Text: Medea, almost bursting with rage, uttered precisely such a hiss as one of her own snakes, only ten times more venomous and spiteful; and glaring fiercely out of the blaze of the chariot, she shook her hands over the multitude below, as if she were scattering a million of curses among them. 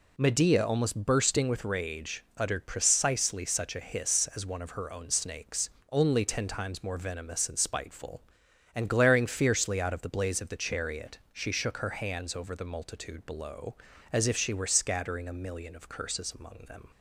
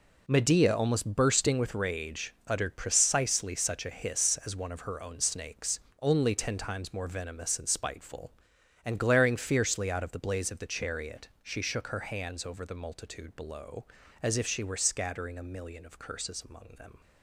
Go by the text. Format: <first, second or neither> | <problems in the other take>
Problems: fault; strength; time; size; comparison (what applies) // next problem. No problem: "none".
first | gets quieter; strong; throughout; 11.5 dB